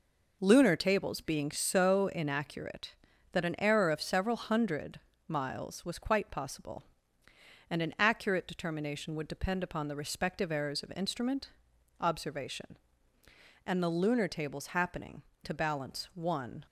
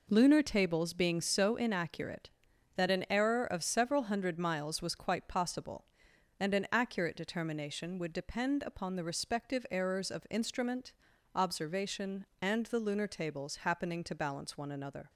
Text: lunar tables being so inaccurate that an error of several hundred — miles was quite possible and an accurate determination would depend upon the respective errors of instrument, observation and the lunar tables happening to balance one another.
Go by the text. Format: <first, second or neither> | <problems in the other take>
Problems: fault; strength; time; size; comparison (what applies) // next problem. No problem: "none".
second | stops before "another"; at 16.6 s